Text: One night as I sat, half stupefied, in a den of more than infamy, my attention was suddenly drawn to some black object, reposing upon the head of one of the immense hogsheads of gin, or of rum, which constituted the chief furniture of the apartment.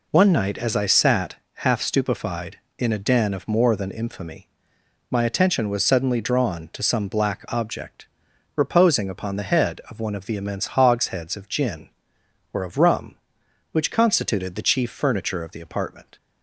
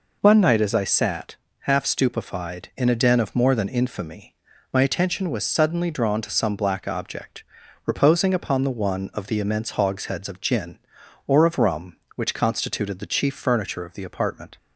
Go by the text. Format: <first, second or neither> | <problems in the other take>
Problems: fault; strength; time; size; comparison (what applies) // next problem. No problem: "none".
first | skips "head of"; at 8.6 s